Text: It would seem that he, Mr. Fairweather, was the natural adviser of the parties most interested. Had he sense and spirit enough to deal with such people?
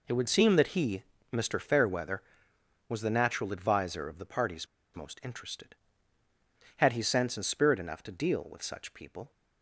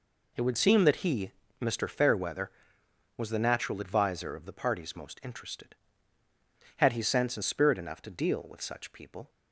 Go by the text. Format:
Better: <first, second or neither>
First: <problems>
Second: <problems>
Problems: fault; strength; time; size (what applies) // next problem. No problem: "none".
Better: second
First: pauses between "parties" and "most"; slight; at 4.6 s; 0.29 s long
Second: none